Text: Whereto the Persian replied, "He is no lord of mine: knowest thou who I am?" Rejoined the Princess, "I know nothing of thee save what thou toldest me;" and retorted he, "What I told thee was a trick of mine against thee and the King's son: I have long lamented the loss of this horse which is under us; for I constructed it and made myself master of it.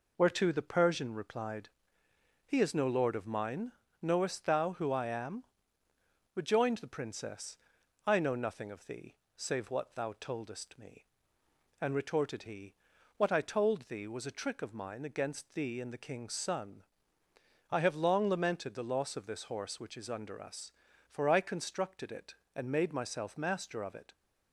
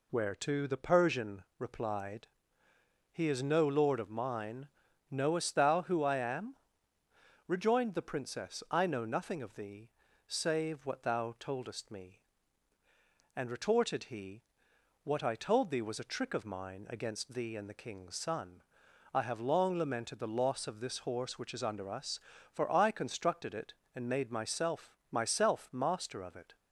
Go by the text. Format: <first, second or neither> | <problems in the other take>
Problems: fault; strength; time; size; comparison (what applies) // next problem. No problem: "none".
first | pauses between "Persian" and "replied"; slight; at 1.4 s; 0.16 s long // pauses between "thee" and "save"; slight; at 9.9 s; 0.34 s long; slight in the first // says "myself" twice; at 25.1 s